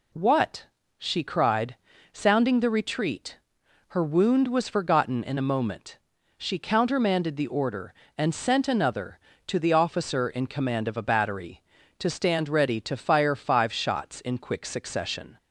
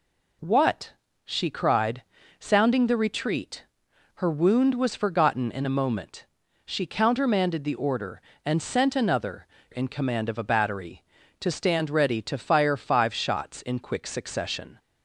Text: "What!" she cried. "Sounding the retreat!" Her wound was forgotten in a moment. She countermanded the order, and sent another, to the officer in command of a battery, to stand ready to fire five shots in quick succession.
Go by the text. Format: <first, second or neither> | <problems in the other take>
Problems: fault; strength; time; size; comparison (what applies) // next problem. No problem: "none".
first | skips "to the officer"; at 9.5 s